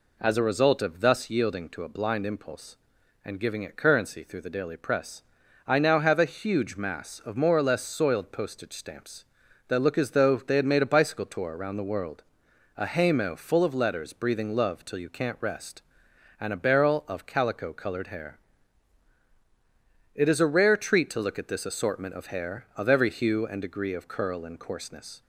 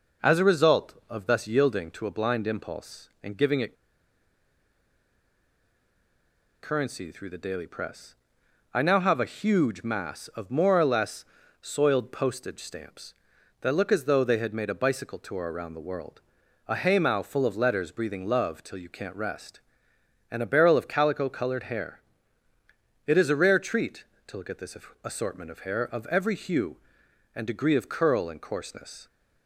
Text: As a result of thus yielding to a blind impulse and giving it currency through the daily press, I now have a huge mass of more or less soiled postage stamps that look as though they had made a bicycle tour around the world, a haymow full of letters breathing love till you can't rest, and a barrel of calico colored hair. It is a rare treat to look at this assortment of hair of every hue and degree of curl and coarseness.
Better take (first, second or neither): first